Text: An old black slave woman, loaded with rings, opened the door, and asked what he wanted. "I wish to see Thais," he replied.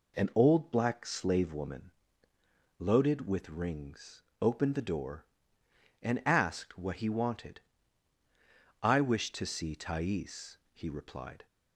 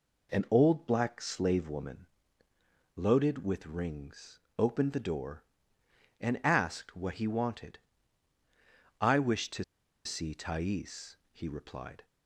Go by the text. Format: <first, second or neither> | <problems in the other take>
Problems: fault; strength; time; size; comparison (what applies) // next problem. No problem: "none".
first | pauses between "to" and "see"; at 9.6 s; 0.41 s long